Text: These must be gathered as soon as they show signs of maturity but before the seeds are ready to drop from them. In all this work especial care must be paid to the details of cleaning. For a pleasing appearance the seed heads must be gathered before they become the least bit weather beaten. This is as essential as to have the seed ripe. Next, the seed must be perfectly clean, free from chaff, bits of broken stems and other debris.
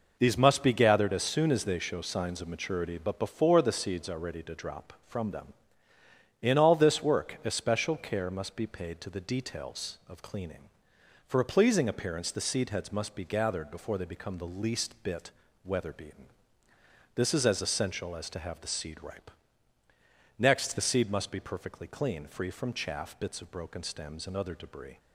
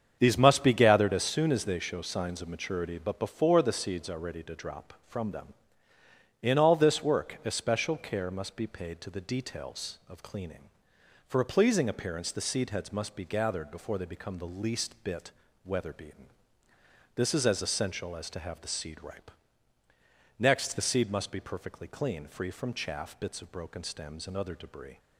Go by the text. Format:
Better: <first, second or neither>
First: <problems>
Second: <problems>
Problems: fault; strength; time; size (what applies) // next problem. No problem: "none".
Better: first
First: pauses between "bit" and "weather"; slight; at 15.3 s; 0.32 s long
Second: starts louder than the rest; strong; until 1.4 s; 7.5 dB // pauses between "bit" and "weather"; slight; at 15.3 s; 0.32 s long